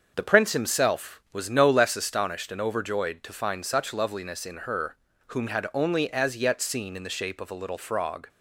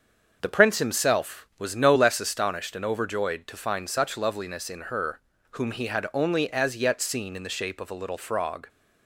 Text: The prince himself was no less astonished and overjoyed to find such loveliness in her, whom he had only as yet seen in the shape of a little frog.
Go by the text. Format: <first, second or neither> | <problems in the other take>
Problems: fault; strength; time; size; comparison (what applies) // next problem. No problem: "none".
second | starts louder than the rest; until 1.1 s; 6.5 dB; also in the second // skips "he"; at 5.4 s